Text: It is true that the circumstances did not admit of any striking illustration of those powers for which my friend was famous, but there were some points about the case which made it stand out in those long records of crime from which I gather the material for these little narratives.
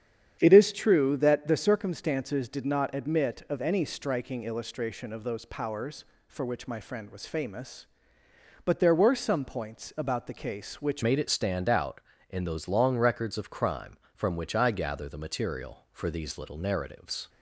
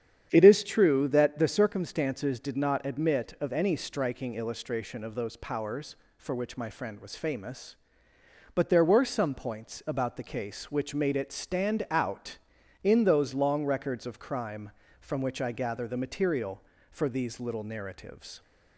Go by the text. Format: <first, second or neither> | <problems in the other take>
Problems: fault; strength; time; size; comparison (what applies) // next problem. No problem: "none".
second | starts louder than the rest; strong; until 1.4 s; 9 dB; strong in the second // changes voice at "made"; from 11.0 s on; 6.2 s long